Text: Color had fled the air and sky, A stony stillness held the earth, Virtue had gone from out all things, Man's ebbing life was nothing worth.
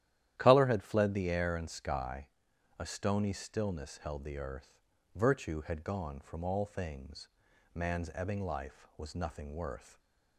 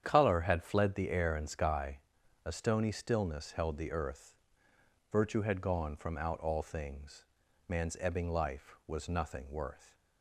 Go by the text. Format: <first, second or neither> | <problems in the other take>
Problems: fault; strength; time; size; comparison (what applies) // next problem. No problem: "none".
second | starts louder than the rest; strong; until 1.3 s; 12 dB; strong in the second // skips "out"; at 6.4 s // stays silent after the last word; slight; from 9.8 s on; 0.5 s long